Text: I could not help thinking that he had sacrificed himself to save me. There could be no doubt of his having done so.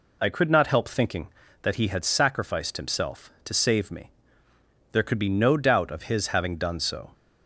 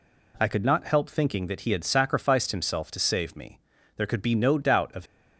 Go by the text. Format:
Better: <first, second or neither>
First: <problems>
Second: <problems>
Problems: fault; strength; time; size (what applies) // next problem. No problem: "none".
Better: first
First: none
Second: stops before "his having done so"; at 5.0 s